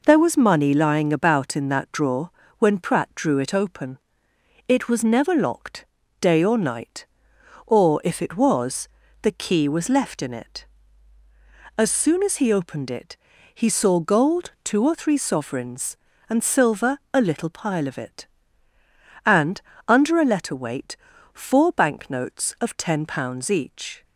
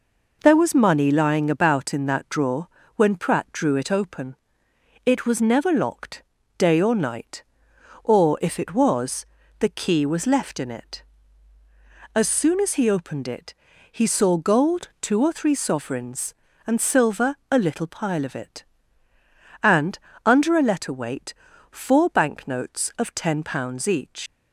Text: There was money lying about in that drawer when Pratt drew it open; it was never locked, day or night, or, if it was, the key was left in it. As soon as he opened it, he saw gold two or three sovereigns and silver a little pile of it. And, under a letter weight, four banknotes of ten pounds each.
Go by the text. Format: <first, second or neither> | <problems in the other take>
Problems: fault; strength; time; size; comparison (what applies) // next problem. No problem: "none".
first | pauses between "drawer" and "when"; slight; at 2.6 s; 0.26 s long; slight in the first // pauses between "silver" and "a"; slight; at 17.3 s; 0.16 s long; slight in the first // leaves "each" unfinished; at 24.2 s; 150 ms